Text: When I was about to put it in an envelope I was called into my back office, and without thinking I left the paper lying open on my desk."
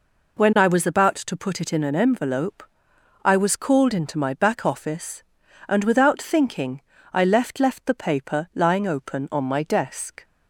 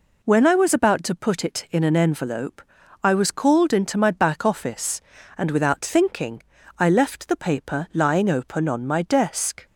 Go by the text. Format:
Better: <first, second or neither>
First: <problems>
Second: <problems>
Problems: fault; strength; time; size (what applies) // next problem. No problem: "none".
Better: second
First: pauses between "envelope" and "I"; noticeable; at 2.6 s; 0.64 s long // pauses between "thinking" and "I"; slight; at 6.7 s; 0.32 s long // says "left" twice; at 7.5 s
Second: pauses between "envelope" and "I"; at 2.6 s; 0.40 s long // pauses between "thinking" and "I"; slight; at 6.4 s; 0.36 s long